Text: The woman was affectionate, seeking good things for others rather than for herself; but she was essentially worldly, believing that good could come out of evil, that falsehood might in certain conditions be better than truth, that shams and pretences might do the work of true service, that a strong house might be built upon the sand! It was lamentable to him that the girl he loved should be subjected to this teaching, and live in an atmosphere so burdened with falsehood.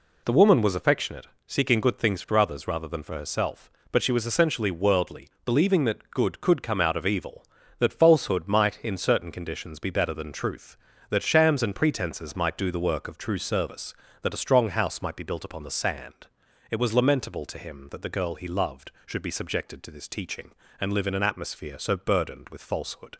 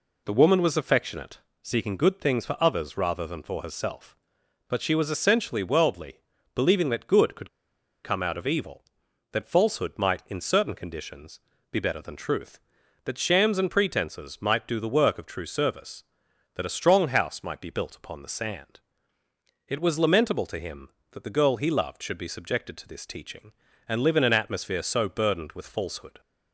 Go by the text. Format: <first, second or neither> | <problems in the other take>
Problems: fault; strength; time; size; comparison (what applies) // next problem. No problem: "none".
first | pauses between "could" and "come"; noticeable; at 7.4 s; 0.54 s long // pauses between "conditions" and "be"; slight; at 11.3 s; 0.32 s long